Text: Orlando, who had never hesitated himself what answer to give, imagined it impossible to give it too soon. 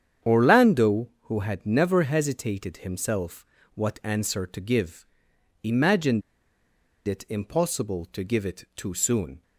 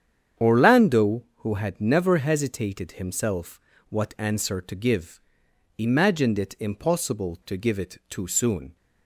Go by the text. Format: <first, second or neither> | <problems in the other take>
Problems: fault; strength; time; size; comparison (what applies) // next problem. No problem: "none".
second | starts louder than the rest; strong; until 1.3 s; 8.5 dB; strong in the second // pauses between "himself" and "what"; slight; at 3.4 s; 0.28 s long; slight in the second // pauses between "imagined" and "it"; noticeable; at 6.2 s; 0.85 s long